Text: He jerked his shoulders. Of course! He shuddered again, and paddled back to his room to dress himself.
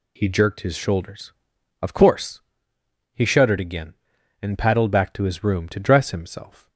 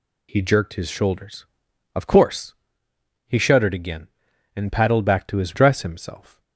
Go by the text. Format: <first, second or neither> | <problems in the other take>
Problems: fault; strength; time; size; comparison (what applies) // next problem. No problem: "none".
first | skips "room to"; at 5.5 s